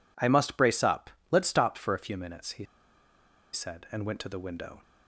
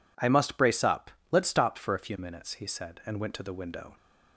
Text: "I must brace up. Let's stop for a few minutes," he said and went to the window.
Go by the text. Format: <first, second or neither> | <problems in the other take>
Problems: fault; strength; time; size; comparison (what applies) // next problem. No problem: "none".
second | pauses between "he" and "said"; noticeable; at 2.6 s; 0.88 s long